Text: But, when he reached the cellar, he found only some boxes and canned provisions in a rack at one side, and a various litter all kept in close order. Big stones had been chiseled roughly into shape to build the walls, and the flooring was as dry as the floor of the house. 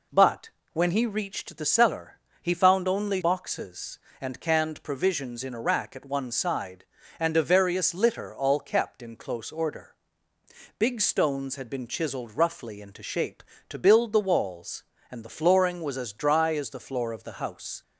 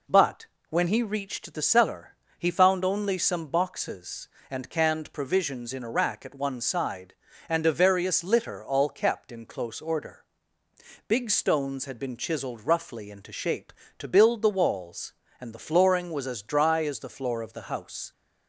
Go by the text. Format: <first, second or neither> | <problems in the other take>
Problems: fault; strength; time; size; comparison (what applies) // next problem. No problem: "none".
second | skips "some"; at 3.2 s